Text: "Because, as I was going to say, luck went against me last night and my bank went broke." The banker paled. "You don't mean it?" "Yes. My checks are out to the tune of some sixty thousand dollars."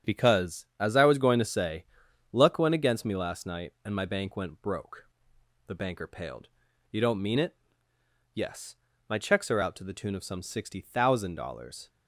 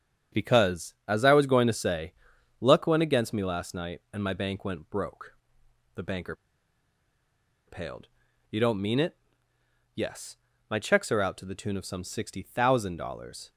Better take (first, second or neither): first